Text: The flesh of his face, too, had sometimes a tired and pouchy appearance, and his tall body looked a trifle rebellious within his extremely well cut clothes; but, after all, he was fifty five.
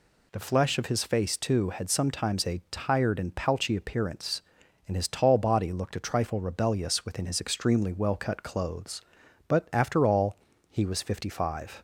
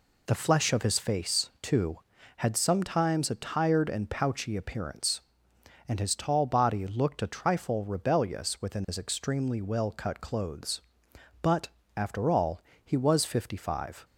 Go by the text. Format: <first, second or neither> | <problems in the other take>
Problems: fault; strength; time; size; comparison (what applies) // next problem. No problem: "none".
neither | none